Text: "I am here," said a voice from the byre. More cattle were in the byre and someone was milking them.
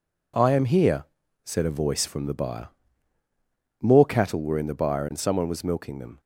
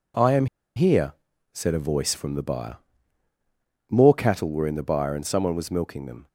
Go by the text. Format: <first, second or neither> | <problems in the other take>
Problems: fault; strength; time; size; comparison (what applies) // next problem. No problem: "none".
first | pauses between "am" and "here"; slight; at 0.4 s; 0.30 s long